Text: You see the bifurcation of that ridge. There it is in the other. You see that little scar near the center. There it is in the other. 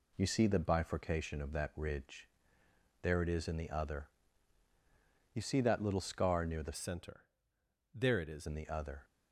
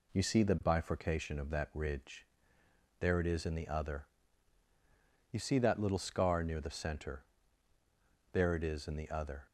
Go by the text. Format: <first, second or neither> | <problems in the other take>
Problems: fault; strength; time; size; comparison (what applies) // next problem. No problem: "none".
second | changes voice from "center" to "is"; from 6.7 to 8.4 s; 1.7 s long